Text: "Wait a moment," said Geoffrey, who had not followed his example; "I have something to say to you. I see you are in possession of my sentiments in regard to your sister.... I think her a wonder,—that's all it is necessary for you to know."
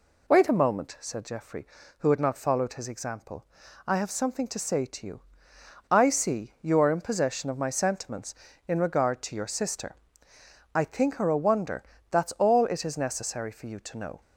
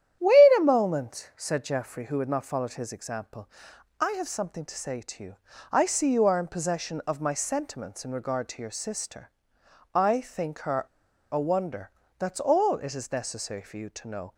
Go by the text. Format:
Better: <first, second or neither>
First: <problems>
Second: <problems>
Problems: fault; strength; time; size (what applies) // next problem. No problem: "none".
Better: first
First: none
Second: starts louder than the rest; strong; until 1.2 s; 10.5 dB // pauses between "her" and "a"; noticeable; at 10.8 s; 0.47 s long